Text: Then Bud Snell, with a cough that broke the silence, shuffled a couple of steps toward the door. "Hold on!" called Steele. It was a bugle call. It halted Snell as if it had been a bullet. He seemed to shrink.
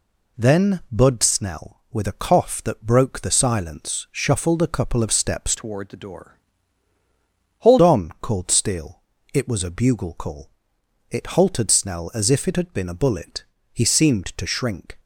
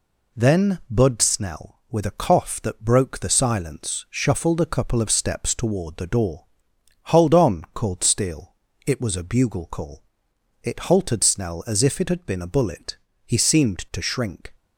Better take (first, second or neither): second